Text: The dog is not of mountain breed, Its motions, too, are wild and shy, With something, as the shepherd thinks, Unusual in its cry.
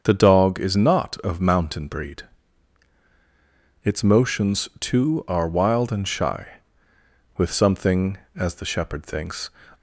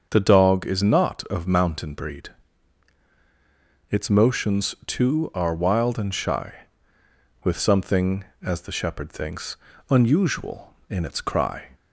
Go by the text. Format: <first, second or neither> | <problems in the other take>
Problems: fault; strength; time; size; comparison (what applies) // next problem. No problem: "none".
second | starts louder than the rest; until 1.0 s; 6.5 dB; also in the second // stops before "Unusual in its cry"; at 9.7 s